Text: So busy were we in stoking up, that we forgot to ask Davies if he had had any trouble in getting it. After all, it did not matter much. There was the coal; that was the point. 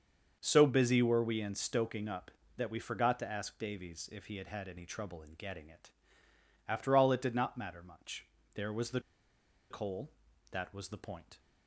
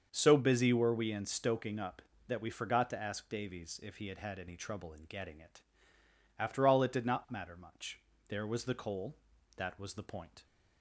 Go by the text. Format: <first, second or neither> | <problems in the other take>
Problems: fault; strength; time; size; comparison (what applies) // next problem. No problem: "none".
second | starts louder than the rest; until 1.4 s; 6.5 dB; also in the second // pauses between "the" and "coal"; noticeable; at 9.0 s; 0.69 s long